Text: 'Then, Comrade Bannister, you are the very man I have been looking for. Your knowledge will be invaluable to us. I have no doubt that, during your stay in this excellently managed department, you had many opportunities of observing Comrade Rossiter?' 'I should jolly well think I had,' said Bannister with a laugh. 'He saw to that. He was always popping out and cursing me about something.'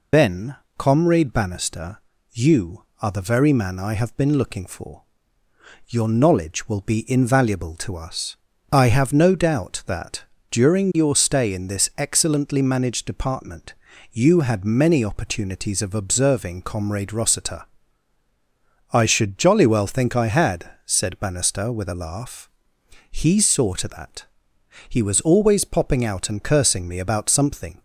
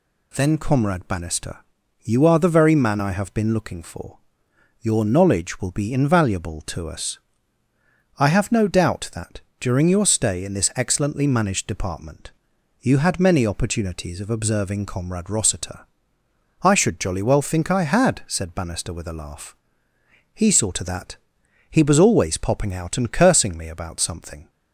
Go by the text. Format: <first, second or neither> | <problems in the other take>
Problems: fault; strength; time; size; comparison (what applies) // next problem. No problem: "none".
second | loses the start of "Then"; at 0.1 s; 75 ms